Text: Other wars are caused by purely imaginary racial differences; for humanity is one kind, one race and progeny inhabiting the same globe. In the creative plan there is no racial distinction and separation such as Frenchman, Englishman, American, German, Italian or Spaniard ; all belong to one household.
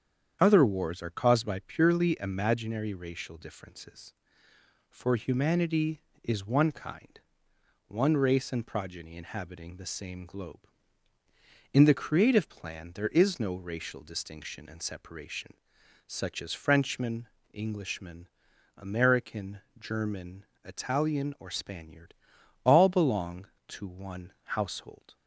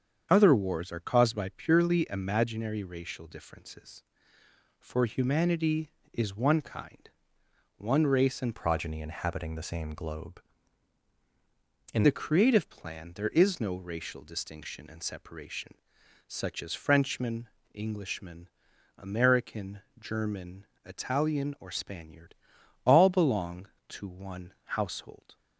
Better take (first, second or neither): first